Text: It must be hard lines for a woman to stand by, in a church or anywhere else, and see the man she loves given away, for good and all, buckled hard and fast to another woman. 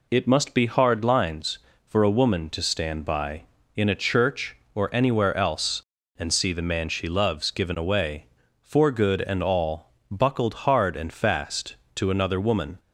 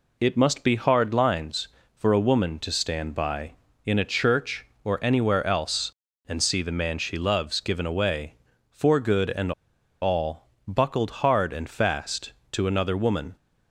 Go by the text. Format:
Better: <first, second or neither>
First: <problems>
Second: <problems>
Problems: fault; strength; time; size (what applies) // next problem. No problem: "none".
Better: first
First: none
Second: pauses between "and" and "all"; noticeable; at 9.5 s; 0.50 s long